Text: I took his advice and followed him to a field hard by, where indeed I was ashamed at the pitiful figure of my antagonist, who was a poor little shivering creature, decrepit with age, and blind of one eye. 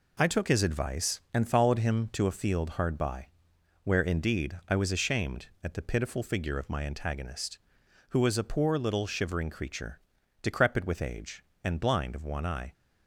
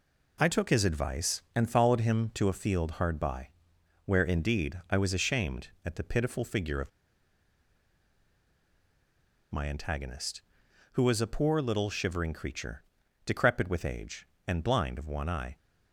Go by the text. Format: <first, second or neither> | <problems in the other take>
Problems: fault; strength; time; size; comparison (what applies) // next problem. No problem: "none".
first | pauses between "of" and "my"; strong; at 6.9 s; 2.6 s long